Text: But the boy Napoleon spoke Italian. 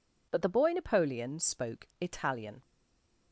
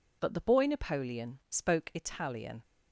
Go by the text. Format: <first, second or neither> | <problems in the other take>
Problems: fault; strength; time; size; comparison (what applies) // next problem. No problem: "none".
second | stays silent after the last word; slight; from 2.6 s on; 0.7 s long